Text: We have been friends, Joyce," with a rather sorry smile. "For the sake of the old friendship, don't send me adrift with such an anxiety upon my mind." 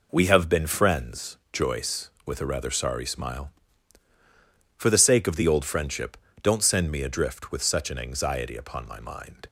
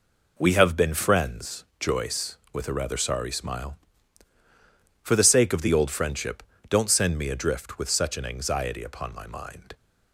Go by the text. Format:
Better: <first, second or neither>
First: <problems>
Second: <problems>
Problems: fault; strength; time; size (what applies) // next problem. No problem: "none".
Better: neither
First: none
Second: none